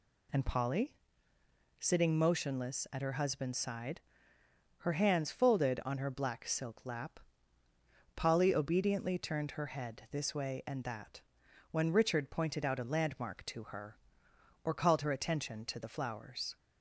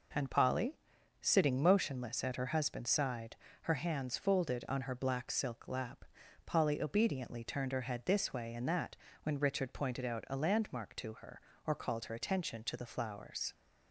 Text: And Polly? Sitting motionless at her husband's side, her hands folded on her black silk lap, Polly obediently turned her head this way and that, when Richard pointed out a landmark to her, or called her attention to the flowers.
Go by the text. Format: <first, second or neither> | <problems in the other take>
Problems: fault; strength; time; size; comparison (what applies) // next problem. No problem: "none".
neither | none